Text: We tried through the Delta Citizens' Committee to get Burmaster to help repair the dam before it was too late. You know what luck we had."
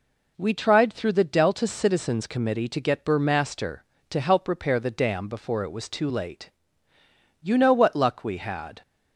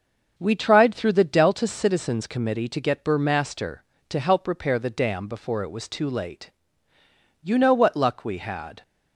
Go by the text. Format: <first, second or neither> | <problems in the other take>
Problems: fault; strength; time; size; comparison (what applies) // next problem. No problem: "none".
first | starts louder than the rest; until 1.7 s; 6.5 dB